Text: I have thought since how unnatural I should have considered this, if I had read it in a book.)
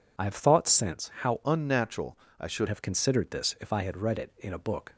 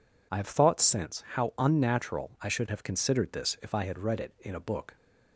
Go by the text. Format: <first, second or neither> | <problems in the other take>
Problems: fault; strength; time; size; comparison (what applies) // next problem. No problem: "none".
second | changes voice from "unnatural" to "should"; from 1.4 to 2.6 s; 1.2 s long // pauses between "unnatural" and "I"; slight; at 2.1 s; 0.22 s long